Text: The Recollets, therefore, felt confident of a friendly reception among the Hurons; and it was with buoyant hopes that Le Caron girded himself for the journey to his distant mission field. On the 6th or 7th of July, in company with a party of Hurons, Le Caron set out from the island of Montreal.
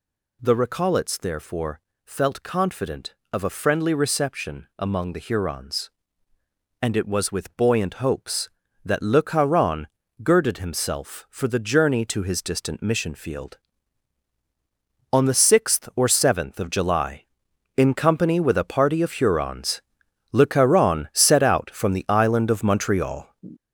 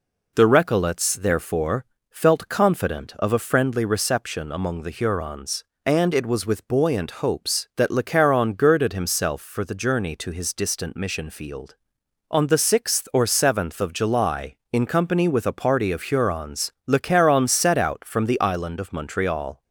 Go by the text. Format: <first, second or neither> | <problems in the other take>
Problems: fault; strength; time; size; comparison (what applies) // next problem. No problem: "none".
second | gets louder; throughout; 7 dB // pauses between "Caron" and "girded"; slight; at 9.8 s; 0.36 s long